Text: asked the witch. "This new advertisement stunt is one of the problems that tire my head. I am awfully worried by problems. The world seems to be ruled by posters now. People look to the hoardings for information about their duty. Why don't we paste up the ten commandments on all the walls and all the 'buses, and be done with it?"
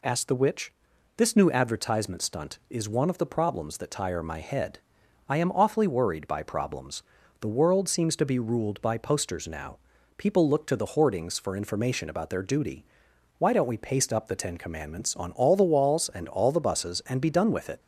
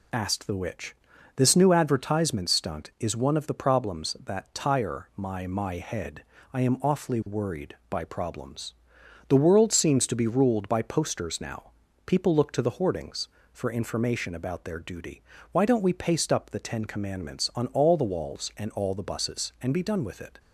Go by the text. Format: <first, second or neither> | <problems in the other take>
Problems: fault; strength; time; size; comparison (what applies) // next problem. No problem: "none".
first | says "my" twice; at 5.4 s